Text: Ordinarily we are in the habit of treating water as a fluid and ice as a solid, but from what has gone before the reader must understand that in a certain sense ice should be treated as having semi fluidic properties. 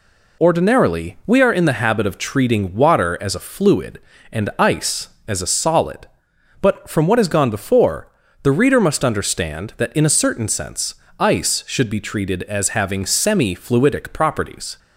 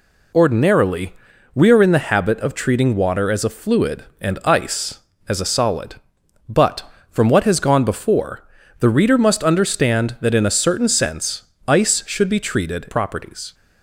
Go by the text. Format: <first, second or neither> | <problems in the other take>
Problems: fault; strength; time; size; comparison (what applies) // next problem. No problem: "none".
first | pauses between "Ordinarily" and "we"; at 1.1 s; 0.42 s long // pauses between "before" and "the"; slight; at 8.4 s; 0.36 s long; slight in the first // pauses between "sense" and "ice"; slight; at 11.4 s; 0.24 s long; slight in the first // skips "as having semi fluidic"; at 12.8 s